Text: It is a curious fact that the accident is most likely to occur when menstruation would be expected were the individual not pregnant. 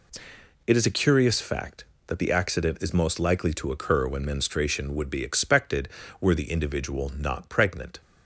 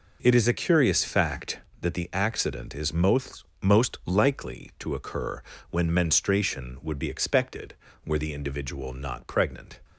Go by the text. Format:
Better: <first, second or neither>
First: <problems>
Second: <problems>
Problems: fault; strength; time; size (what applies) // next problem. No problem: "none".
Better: first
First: none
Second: says "most" twice; at 3.6 s // pauses between "occur" and "when"; slight; at 5.4 s; 0.30 s long